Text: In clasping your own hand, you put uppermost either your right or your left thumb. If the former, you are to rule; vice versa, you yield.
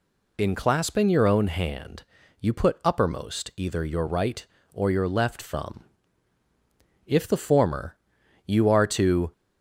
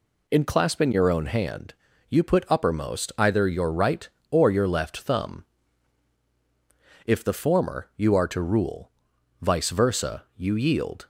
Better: second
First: stops before "rule vice versa you yield"; at 9.3 s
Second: none

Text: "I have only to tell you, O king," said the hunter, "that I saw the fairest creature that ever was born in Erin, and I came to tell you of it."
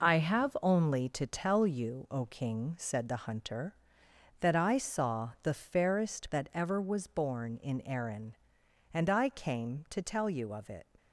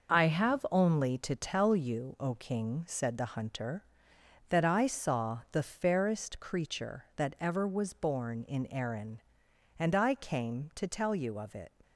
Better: second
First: skips "creature"; at 6.3 s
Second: none

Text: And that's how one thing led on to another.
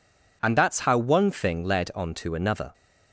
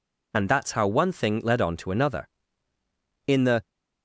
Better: first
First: none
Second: goes on to say "In the"; slight; from 3.2 s on; 0.42 s long

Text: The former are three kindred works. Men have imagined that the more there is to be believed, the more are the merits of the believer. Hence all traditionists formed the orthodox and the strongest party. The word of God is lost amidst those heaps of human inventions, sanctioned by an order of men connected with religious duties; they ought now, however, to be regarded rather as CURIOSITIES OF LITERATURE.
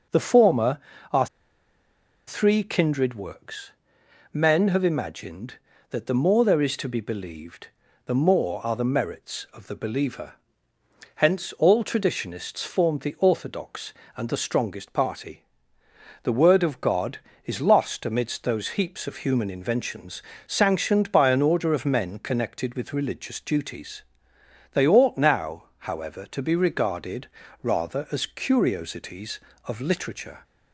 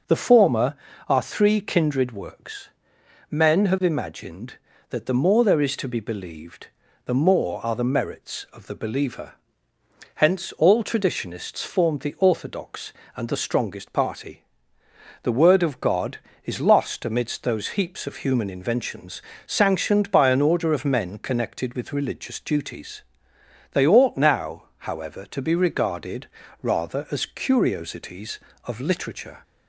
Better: second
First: pauses between "are" and "three"; at 1.2 s; 1.0 s long // pauses between "regarded" and "rather"; slight; at 27.2 s; 0.34 s long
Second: pauses between "regarded" and "rather"; slight; at 26.2 s; 0.34 s long

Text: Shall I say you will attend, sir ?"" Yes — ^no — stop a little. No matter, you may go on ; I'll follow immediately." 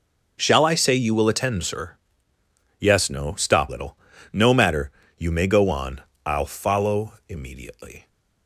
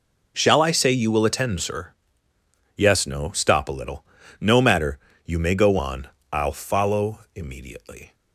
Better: second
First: skips "a"; at 3.6 s // pauses between "follow" and "immediately"; slight; at 7.1 s; 0.16 s long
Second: pauses between "follow" and "immediately"; slight; at 7.2 s; 0.16 s long

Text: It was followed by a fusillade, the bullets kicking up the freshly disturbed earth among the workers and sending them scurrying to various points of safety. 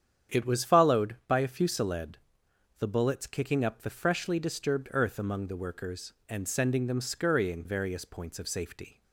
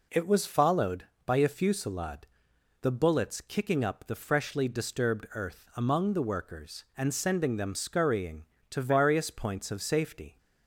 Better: second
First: starts louder than the rest; strong; until 1.3 s; 8.5 dB // skips "to"; at 7.6 s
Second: none

